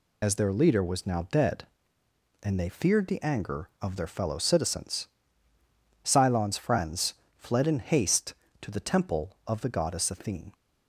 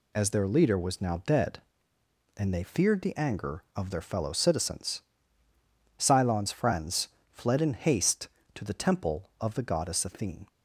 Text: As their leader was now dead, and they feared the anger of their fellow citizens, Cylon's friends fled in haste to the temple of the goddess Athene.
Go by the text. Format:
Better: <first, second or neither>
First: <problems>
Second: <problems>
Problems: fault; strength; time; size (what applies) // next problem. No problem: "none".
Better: second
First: loses the start of "As"; at 0.2 s; 20 ms // pauses between "friends" and "fled"; slight; at 7.1 s; 0.22 s long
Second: pauses between "friends" and "fled"; slight; at 7.0 s; 0.22 s long